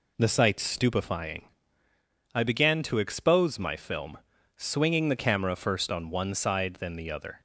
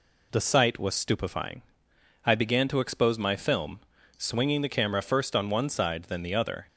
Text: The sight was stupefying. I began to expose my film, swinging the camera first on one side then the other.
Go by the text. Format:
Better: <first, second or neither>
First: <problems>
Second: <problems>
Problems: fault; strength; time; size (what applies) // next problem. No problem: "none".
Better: second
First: skips "was"; at 0.6 s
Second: none